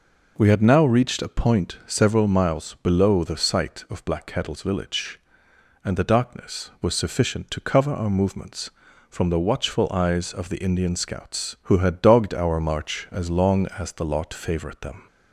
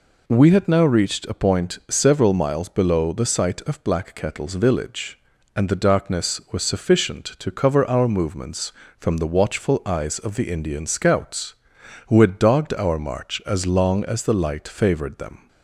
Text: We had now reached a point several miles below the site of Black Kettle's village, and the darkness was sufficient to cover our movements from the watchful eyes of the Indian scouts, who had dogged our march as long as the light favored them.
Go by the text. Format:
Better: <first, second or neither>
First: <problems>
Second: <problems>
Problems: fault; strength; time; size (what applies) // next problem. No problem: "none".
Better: second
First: says "lot" for "light"; at 14.0 s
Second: none